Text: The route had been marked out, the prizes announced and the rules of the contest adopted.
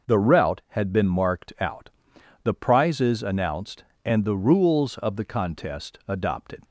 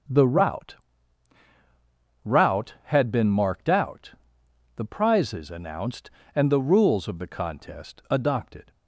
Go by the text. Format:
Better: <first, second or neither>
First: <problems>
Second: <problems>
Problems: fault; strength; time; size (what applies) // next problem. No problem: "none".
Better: first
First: none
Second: starts louder than the rest; until 2.5 s; 7 dB // says "route" twice; at 2.2 s